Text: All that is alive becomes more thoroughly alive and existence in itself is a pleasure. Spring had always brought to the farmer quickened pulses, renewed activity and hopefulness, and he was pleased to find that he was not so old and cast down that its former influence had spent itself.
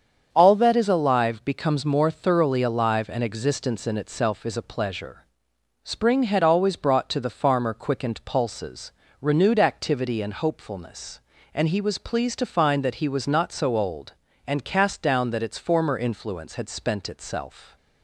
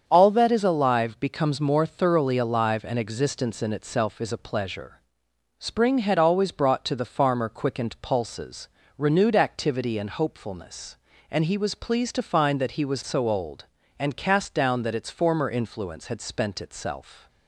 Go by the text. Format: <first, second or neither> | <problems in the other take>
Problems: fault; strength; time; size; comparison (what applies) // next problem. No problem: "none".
first | starts louder than the rest; strong; until 1.0 s; 7.5 dB; strong in the first // skips "not"; at 13.0 s